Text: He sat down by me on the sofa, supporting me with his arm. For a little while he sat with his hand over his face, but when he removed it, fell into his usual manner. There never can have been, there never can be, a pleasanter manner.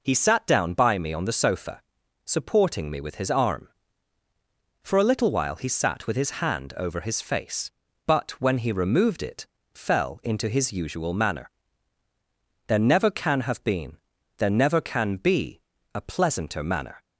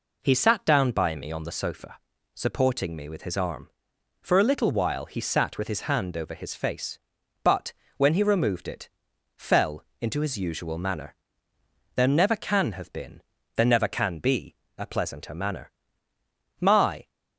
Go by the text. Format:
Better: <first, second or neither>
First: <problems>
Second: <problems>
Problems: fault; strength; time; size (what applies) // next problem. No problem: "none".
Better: first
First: none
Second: pauses between "but" and "when"; slight; at 7.7 s; 0.26 s long // pauses between "fell" and "into"; slight; at 9.8 s; 0.20 s long // goes on to say "My"; from 16.5 s on; 0.50 s long